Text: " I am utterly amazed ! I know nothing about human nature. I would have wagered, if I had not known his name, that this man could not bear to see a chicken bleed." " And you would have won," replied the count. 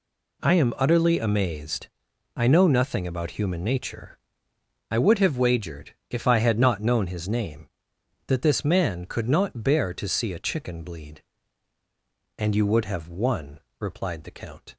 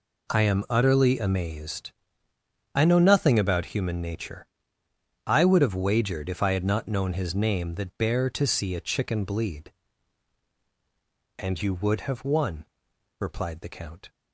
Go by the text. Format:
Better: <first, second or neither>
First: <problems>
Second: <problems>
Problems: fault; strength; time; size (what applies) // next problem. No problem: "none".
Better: first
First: none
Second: skips "this man could not"; at 7.9 s